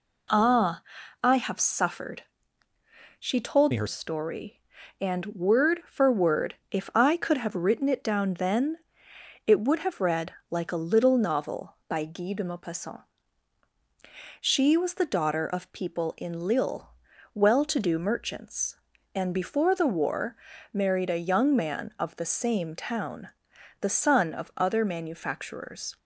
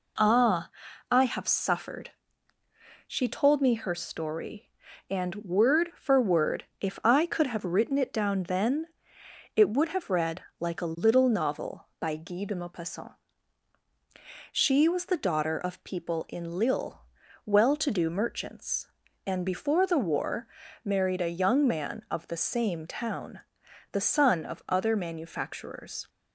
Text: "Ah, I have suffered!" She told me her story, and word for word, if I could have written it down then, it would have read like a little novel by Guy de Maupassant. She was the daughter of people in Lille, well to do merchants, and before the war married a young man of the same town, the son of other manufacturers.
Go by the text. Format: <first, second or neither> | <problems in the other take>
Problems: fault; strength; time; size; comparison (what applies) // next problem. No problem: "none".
second | changes voice from "me" to "her"; from 3.7 to 3.8 s; 0.1 s long // pauses between "read" and "like"; slight; at 10.3 s; 0.18 s long; slight in the second // pauses between "war" and "married"; slight; at 20.3 s; 0.34 s long; slight in the second